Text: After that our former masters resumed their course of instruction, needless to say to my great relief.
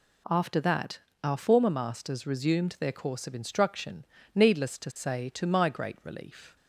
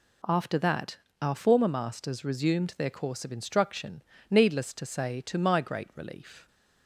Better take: neither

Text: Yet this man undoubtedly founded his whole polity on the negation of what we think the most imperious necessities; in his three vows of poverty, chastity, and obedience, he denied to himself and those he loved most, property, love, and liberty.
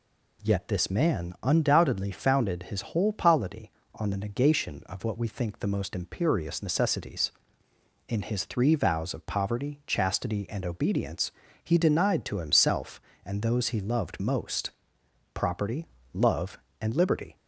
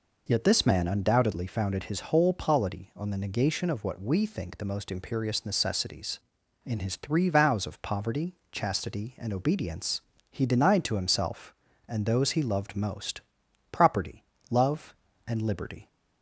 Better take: neither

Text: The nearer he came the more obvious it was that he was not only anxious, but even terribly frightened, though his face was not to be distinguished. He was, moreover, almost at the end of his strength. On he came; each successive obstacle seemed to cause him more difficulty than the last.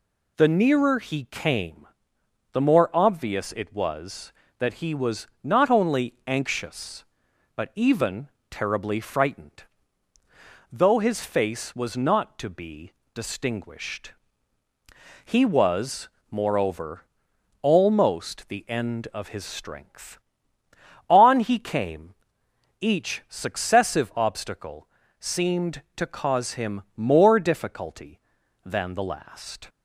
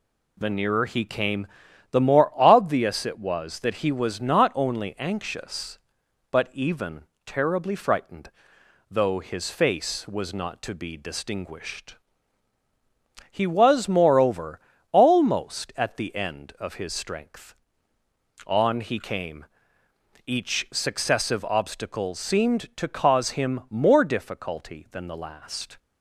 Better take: second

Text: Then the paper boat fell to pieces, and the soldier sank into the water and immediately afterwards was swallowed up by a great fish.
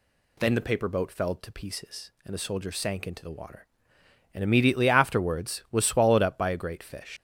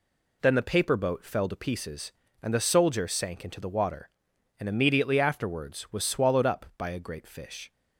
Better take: second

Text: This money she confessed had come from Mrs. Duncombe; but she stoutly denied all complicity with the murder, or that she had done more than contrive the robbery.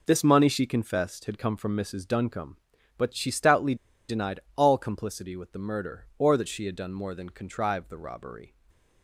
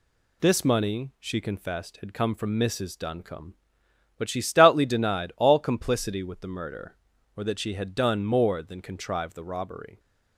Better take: second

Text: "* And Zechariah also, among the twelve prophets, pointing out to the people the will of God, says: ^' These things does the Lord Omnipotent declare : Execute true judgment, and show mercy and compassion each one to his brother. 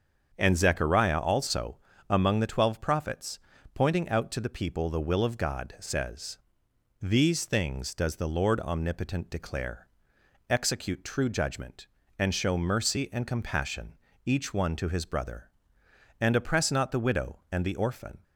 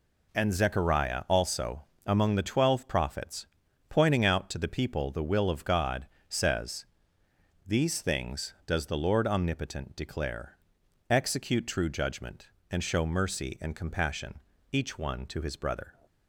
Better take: second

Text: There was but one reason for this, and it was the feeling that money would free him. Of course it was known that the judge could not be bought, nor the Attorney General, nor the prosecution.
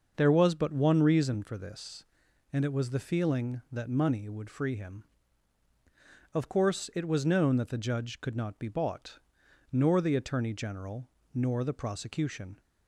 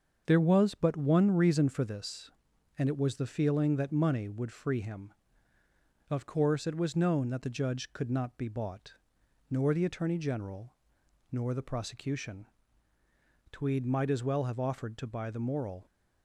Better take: first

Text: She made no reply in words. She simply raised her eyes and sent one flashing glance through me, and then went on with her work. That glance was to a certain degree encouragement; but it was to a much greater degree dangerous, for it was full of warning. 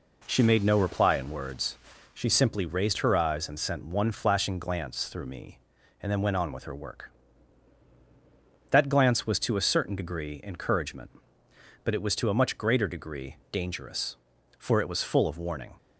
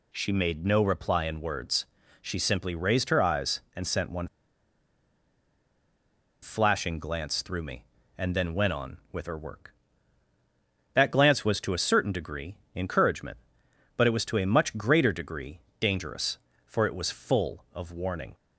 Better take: first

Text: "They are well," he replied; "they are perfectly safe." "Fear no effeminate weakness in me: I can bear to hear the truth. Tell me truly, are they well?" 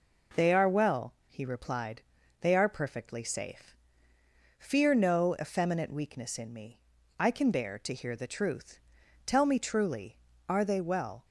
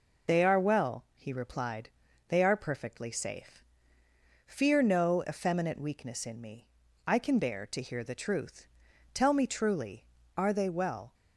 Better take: first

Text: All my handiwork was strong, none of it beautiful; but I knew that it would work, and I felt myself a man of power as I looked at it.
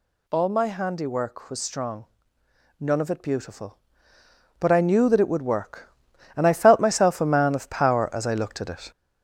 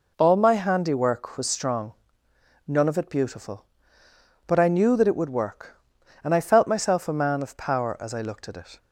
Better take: second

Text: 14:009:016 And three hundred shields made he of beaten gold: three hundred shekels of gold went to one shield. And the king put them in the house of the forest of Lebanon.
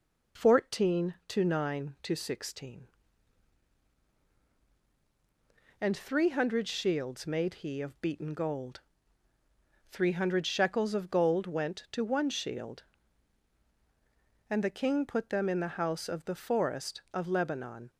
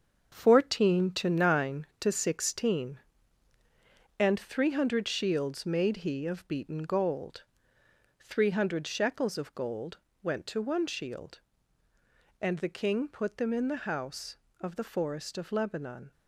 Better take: first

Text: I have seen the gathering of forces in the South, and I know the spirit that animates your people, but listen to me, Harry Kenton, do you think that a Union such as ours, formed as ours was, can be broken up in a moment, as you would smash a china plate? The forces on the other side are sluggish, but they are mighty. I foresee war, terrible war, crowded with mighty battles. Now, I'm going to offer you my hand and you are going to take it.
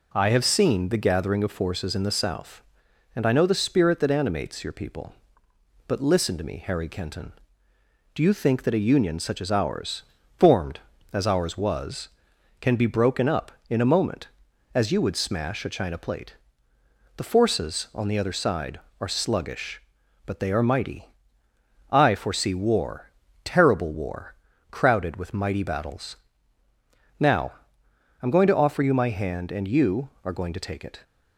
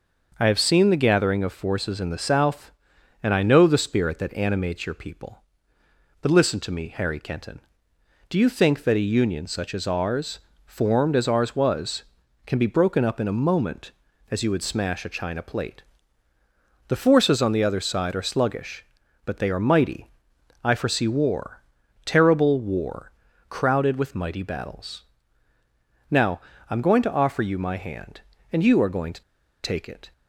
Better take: first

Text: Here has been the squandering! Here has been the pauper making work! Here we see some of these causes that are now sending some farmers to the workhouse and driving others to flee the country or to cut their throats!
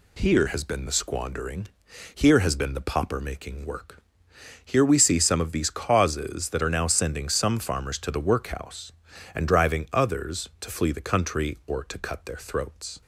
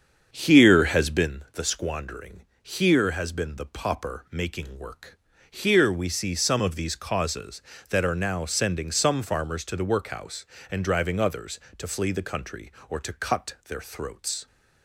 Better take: first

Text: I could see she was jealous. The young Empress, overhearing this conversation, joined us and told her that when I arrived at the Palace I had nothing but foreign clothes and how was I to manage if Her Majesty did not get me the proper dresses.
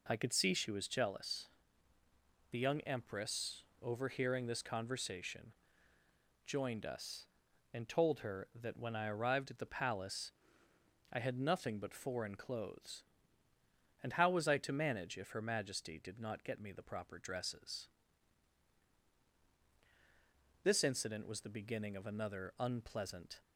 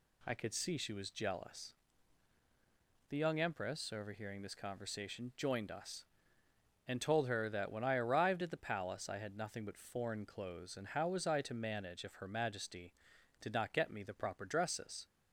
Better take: second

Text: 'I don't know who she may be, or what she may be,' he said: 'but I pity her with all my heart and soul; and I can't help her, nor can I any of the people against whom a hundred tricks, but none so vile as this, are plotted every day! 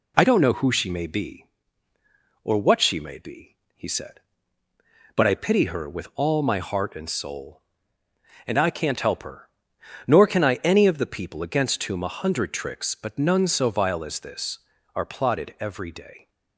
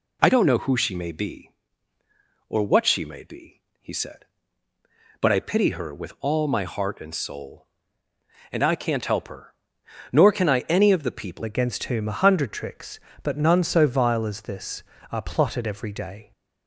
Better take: first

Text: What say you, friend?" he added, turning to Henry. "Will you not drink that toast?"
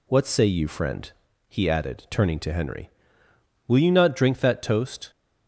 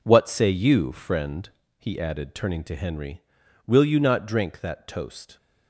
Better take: first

